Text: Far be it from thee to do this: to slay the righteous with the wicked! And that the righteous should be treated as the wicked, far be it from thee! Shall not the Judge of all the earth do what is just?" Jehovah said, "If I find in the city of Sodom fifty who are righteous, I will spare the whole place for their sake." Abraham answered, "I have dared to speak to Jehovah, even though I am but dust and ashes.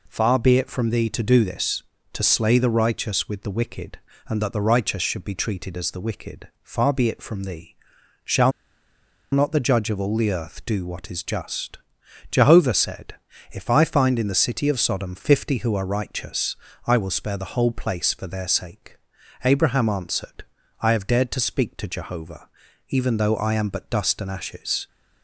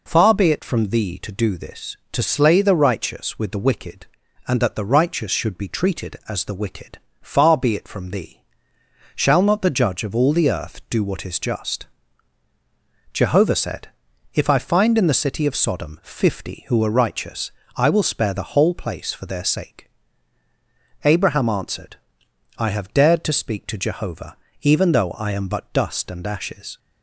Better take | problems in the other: second | pauses between "Shall" and "not"; noticeable; at 8.5 s; 0.81 s long

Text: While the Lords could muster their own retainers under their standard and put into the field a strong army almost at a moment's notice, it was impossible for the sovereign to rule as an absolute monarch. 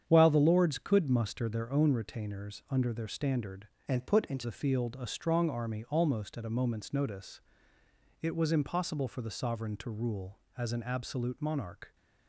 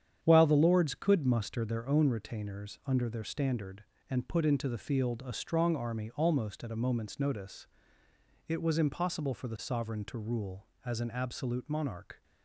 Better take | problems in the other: second | starts louder than the rest; strong; until 1.0 s; 8.5 dB; strong in the second // changes voice from "and" to "into"; from 3.8 to 4.4 s; 0.6 s long

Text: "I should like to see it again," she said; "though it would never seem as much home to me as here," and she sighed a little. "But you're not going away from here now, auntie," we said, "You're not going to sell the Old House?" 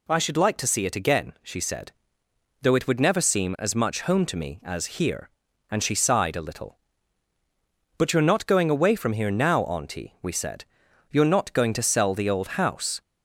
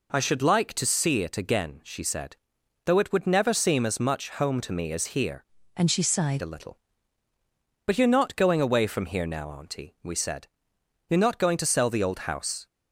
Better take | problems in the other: first | changes voice from "and" to "sighed"; from 5.7 to 6.4 s; 0.7 s long

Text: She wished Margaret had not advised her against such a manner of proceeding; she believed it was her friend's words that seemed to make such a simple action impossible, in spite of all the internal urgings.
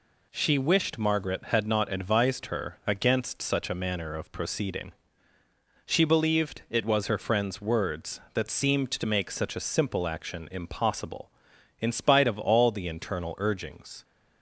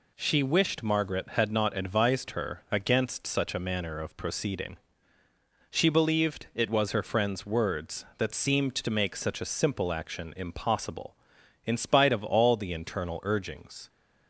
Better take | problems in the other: neither | none

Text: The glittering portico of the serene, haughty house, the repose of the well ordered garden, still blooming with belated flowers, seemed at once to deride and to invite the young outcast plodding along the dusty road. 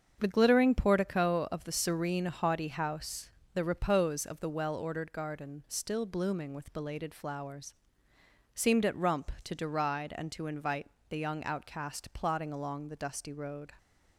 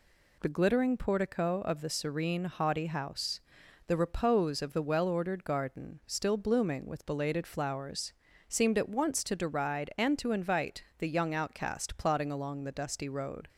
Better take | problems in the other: second | starts louder than the rest; until 1.2 s; 7 dB // says "rump" for "once"; at 8.9 s // pauses between "invite" and "the"; slight; at 10.8 s; 0.20 s long

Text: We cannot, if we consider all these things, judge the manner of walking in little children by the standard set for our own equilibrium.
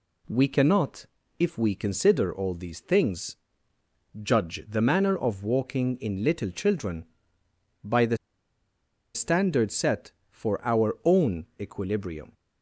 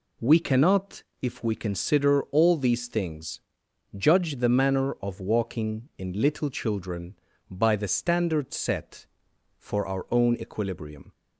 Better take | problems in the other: second | pauses between "the" and "standard"; noticeable; at 8.1 s; 0.97 s long // pauses between "own" and "equilibrium"; slight; at 11.4 s; 0.16 s long

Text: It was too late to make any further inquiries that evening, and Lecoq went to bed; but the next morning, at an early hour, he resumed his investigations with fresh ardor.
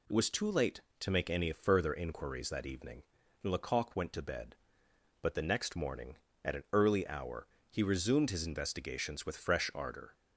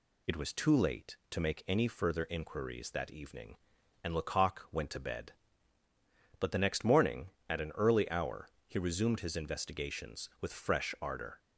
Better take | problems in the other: neither | none

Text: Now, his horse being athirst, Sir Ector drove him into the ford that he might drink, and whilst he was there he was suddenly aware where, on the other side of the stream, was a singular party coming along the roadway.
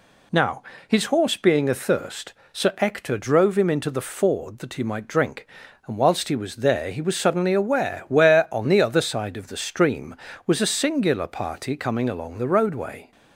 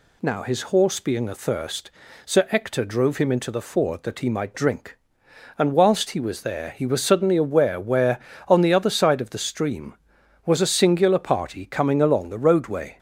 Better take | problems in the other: neither | none

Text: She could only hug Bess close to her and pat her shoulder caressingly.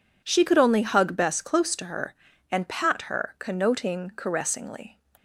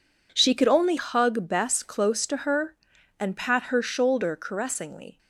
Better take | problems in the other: second | says "connoting" for "shoulder"; at 3.3 s

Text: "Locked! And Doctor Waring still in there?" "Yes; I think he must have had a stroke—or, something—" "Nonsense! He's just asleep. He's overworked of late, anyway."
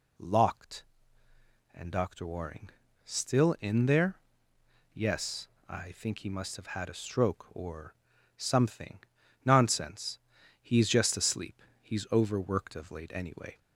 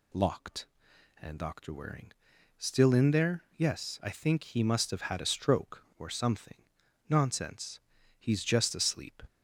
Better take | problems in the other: first | pauses between "Waring" and "still"; noticeable; at 2.1 s; 0.46 s long; slight in the first // stops before "He's overworked of late anyway"; at 9.2 s

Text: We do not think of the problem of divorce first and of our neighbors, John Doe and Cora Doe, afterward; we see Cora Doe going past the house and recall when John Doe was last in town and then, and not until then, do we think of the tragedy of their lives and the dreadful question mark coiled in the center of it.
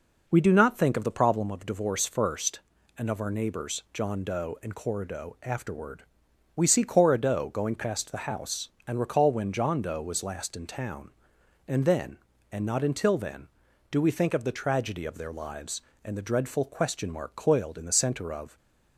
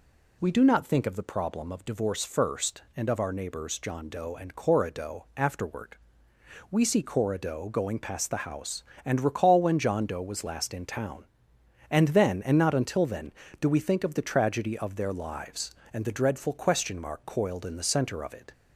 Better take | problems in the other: second | stops before "it"; at 18.5 s

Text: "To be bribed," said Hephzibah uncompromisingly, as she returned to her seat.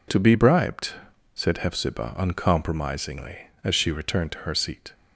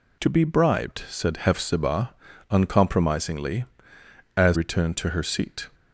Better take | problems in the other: first | pauses between "Hephzibah" and "uncompromisingly"; at 2.1 s; 0.38 s long // skips "she"; at 4.5 s

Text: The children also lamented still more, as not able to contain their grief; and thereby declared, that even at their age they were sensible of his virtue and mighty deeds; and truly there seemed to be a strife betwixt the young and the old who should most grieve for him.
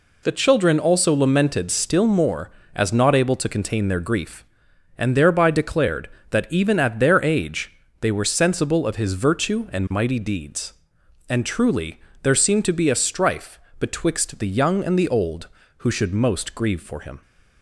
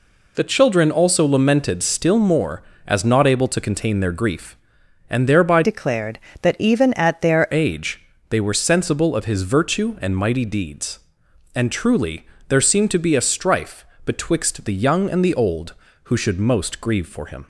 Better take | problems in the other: first | changes voice from "declared" to "their"; from 5.6 to 7.4 s; 1.8 s long // pauses between "age" and "they"; slight; at 8.0 s; 0.24 s long; slight in the first // pauses between "truly" and "there"; slight; at 12.2 s; 0.22 s long; slight in the first // pauses between "strife" and "betwixt"; slight; at 13.8 s; 0.22 s long; slight in the first

